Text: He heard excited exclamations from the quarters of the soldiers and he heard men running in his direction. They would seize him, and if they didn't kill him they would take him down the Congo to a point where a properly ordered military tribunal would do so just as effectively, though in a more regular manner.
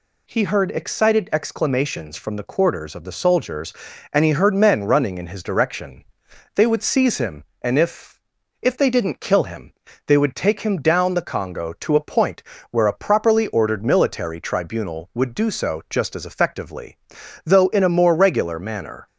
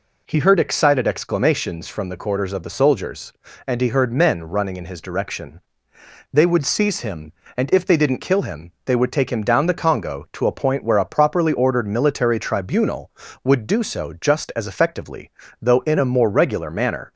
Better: second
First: says "if" twice; at 8.6 s // pauses between "him" and "they"; slight; at 9.7 s; 0.36 s long // pauses between "point" and "where"; slight; at 12.4 s; 0.30 s long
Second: none

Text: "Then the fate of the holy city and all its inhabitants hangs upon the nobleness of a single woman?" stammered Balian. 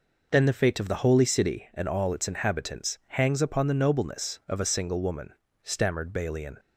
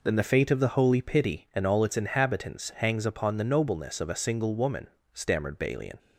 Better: first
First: none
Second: says "pity" for "city"; at 1.0 s

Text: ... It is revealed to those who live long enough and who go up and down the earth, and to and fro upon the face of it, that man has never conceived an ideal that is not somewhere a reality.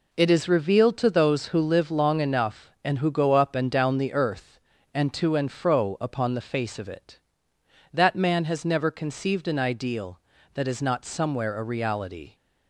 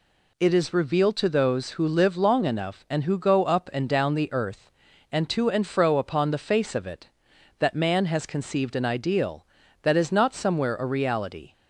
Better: first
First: none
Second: skips "never"; at 8.2 s

